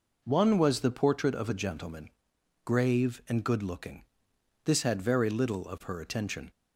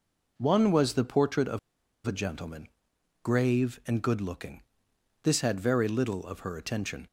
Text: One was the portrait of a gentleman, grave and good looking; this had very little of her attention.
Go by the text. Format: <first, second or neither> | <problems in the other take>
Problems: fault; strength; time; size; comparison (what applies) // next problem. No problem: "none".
first | pauses between "of" and "a"; noticeable; at 1.5 s; 0.47 s long